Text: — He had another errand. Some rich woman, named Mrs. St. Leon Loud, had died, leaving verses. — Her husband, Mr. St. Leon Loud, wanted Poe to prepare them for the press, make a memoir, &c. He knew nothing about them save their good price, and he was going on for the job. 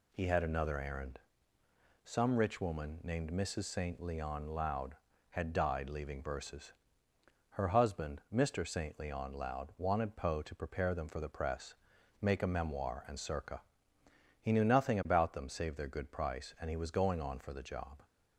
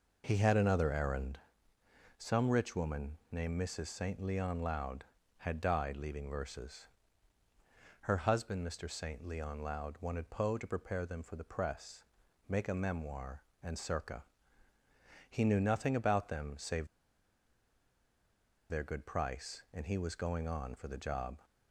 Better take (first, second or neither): first